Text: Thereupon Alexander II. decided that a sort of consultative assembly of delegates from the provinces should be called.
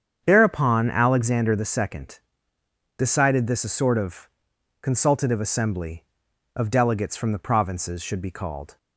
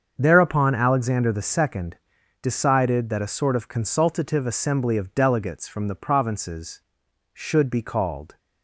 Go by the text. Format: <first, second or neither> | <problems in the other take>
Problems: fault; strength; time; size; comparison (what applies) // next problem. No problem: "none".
second | starts louder than the rest; strong; until 1.2 s; 8 dB; also in the second // says "this" for "that"; at 3.4 s // pauses between "of" and "consultative"; noticeable; at 4.2 s; 0.52 s long